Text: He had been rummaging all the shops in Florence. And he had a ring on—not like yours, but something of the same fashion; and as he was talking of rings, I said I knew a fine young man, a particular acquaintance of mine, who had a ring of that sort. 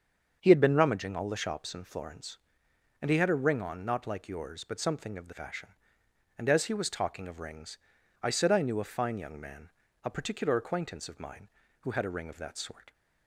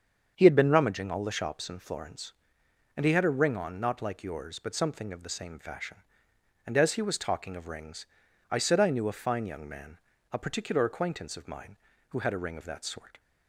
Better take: second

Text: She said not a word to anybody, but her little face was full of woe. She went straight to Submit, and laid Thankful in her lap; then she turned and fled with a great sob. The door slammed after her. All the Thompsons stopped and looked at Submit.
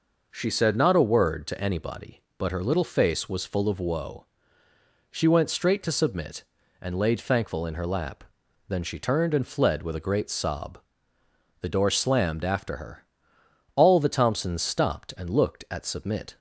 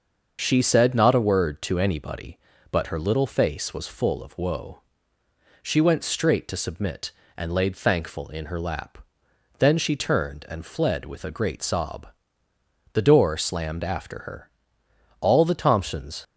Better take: first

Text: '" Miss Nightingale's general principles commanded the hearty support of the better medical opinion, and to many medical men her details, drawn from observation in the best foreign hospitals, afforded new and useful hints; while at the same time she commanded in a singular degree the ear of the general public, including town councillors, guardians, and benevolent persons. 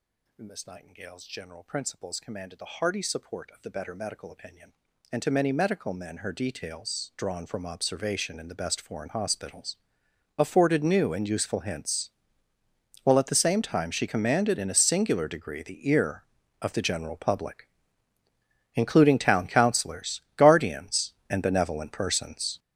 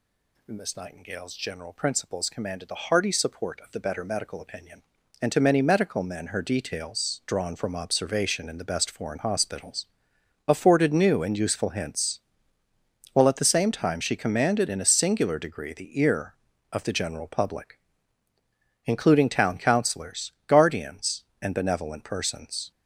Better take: second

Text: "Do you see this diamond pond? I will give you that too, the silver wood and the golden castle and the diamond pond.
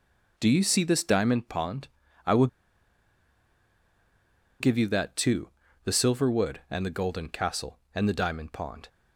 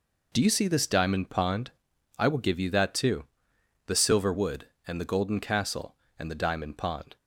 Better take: second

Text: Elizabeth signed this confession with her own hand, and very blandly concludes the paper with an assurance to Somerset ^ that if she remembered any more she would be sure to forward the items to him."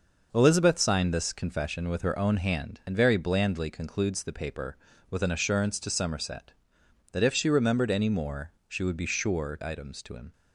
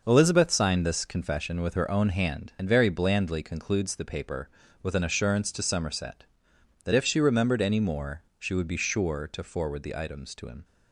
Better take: second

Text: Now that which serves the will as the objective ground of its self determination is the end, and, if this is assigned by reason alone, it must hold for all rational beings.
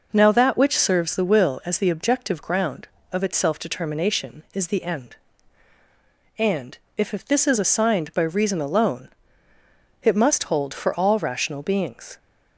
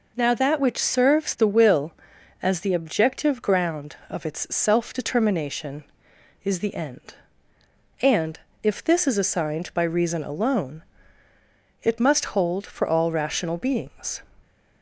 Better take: second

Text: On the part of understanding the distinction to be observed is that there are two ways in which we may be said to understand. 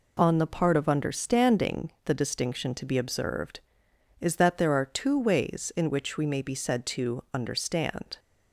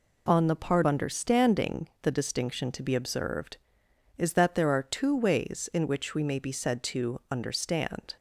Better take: first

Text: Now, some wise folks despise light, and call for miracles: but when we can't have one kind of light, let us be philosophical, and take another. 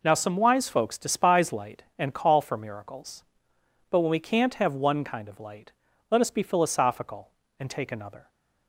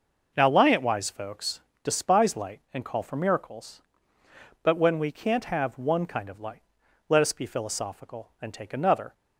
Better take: first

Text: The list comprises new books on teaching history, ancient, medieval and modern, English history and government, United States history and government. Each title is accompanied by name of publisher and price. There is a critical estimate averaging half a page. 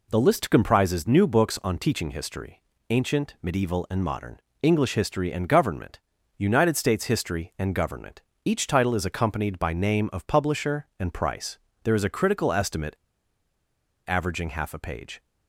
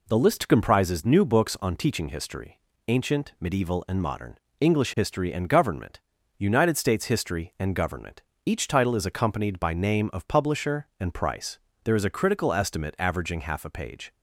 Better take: second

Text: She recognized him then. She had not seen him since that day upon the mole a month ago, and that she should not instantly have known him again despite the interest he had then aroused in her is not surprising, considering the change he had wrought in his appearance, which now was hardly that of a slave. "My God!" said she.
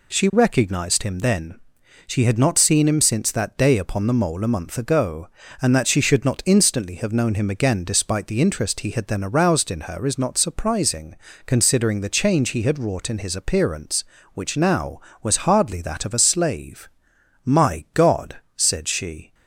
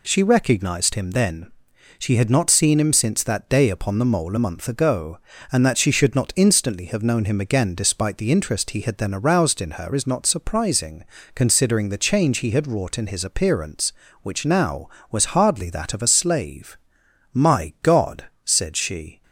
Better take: neither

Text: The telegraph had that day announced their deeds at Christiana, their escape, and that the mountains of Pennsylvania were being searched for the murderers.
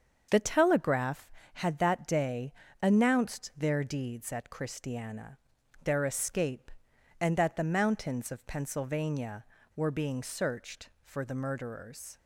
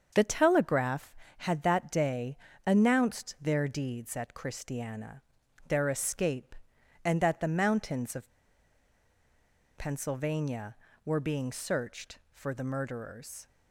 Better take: first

